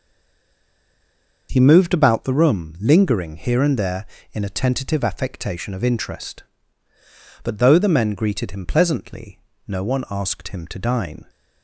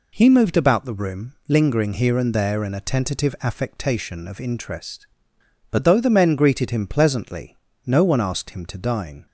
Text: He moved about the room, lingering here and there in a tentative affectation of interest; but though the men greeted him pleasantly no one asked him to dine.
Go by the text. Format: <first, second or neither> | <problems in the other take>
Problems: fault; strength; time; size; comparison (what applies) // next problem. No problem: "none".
second | stays silent before the first word; noticeable; until 1.4 s; 1.4 s long // pauses between "pleasantly" and "no"; slight; at 9.4 s; 0.26 s long; slight in the second